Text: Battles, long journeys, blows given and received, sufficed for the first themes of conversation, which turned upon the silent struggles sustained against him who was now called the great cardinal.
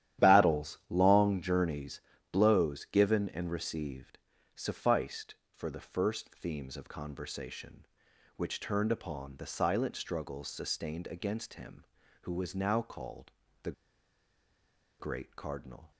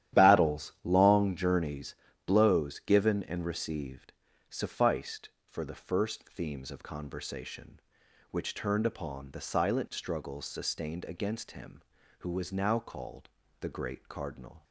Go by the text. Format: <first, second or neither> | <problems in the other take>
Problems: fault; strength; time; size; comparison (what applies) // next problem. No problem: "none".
second | starts louder than the rest; strong; until 1.3 s; 12 dB; strong in the second // pauses between "called" and "the"; slight; at 13.3 s; 0.32 s long; slight in the second // pauses between "the" and "great"; strong; at 13.7 s; 1.2 s long